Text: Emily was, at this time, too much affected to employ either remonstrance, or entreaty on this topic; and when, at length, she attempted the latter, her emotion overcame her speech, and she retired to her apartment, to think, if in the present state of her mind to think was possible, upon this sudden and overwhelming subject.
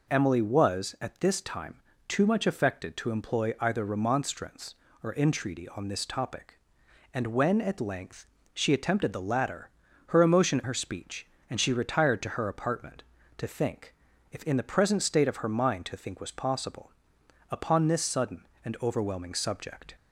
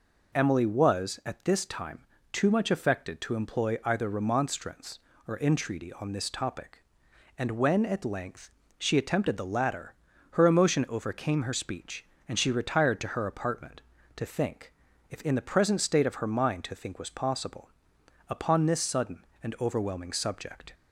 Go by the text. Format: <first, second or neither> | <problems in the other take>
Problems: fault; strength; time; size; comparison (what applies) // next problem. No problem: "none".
second | skips "overcame"; at 10.6 s